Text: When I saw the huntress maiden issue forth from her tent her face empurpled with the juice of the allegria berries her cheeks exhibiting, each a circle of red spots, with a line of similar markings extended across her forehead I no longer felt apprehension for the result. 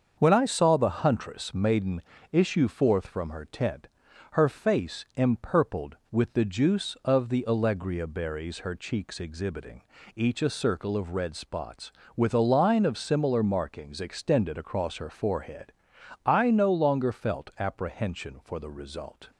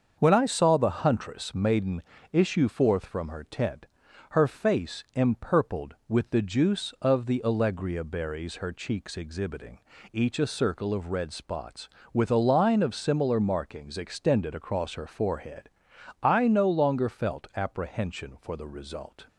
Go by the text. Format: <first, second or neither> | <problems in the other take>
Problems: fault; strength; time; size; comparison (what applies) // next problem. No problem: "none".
neither | starts louder than the rest; the same in both // pauses between "maiden" and "issue"; slight; the same in both // pauses between "tent" and "her"; noticeable; the same in both // pauses between "forehead" and "I"; noticeable; the same in both